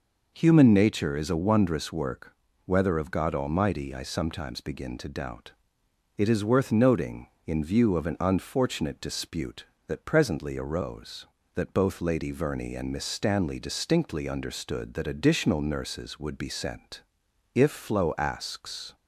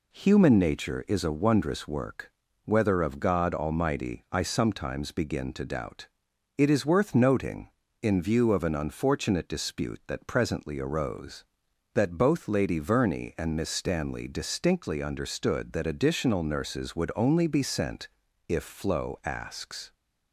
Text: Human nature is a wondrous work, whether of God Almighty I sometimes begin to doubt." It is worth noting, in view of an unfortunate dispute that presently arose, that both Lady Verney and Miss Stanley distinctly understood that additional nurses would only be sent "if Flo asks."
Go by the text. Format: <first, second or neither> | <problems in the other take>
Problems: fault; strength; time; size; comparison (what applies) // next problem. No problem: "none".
second | skips "only"; at 16.3 s // pauses between "sent" and "if"; noticeable; at 17.0 s; 0.50 s long; also in the second